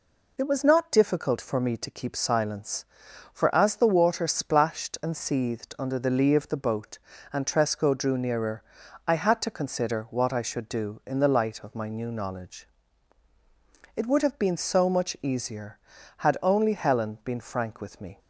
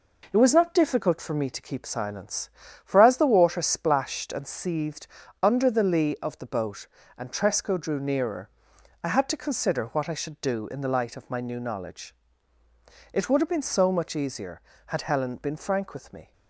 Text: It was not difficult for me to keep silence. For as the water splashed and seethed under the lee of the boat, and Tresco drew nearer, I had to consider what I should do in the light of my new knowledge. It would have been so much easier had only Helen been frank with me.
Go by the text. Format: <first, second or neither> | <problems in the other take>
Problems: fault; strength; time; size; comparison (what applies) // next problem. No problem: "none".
first | pauses between "seethed" and "under"; slight; at 5.0 s; 0.36 s long // skips "only"; at 15.0 s